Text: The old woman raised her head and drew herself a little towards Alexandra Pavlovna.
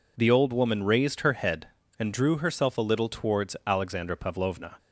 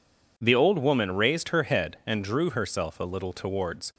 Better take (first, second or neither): first